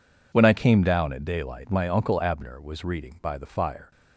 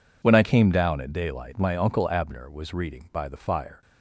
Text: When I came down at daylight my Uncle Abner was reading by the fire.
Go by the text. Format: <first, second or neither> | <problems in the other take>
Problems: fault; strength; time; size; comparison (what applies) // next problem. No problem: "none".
neither | none